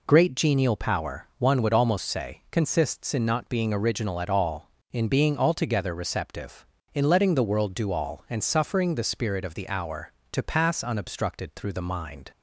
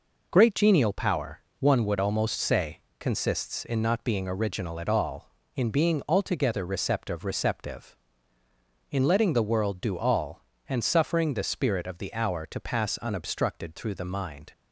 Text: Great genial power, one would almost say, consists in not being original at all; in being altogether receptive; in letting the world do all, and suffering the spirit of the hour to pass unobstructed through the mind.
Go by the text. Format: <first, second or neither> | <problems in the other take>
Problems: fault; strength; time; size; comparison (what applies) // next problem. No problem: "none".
first | says "receptive" twice; at 7.2 s